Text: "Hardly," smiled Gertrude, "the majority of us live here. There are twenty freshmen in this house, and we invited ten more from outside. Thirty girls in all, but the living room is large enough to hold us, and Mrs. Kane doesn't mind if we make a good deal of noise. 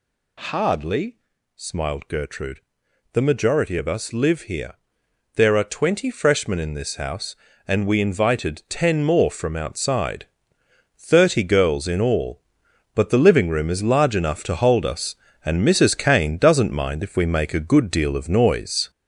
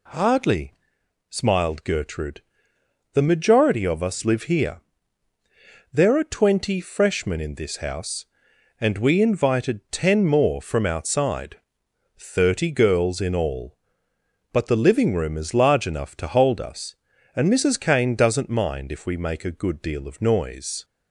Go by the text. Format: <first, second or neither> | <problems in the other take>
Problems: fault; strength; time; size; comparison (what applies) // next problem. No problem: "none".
second | gets louder; noticeable; throughout; 5 dB